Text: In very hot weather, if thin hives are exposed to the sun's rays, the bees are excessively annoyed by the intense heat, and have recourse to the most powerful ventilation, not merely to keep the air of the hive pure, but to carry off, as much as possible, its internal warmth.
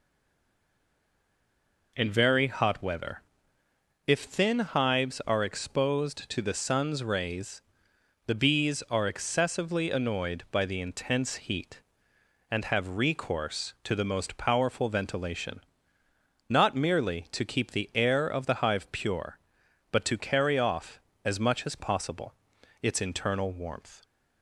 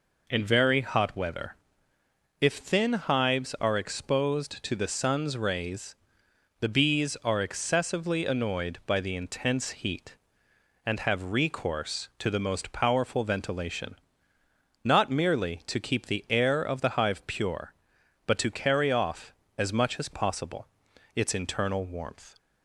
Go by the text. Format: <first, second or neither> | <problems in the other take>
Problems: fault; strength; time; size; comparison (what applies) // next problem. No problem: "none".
second | stays silent before the first word; noticeable; until 1.9 s; 1.9 s long